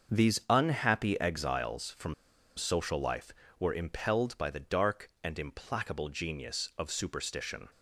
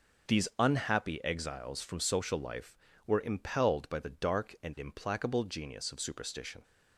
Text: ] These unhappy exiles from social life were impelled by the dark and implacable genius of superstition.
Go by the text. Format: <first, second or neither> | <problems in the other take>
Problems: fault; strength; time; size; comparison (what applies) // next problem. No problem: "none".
second | starts louder than the rest; until 1.2 s; 6.5 dB // pauses between "from" and "social"; at 2.1 s; 0.44 s long